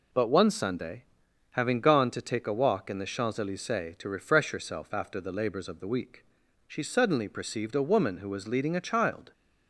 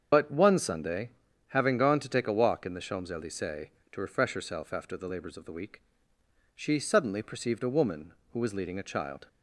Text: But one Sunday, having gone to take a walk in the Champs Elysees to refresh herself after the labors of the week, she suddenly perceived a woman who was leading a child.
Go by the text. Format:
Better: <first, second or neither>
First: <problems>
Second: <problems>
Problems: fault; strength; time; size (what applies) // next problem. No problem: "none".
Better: first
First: none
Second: loses the start of "But"; at 0.1 s; 90 ms // starts louder than the rest; until 1.5 s; 7 dB